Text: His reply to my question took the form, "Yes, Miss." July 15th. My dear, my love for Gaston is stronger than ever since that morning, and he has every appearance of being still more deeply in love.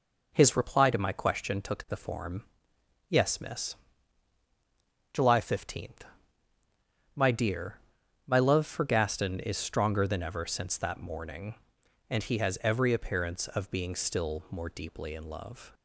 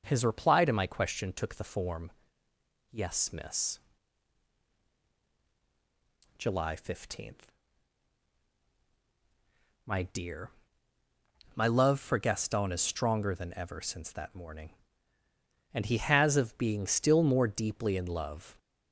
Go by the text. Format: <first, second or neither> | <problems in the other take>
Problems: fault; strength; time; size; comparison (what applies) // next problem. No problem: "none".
first | starts louder than the rest; until 1.0 s; 6.5 dB // skips "every appearance"; at 16.3 s